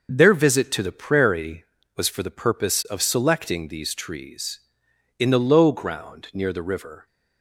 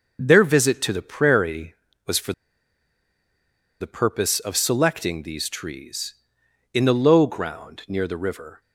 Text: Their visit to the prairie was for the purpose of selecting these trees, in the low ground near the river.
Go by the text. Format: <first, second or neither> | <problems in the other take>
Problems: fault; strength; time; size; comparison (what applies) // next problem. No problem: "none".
first | pauses between "for" and "the"; strong; at 2.3 s; 1.4 s long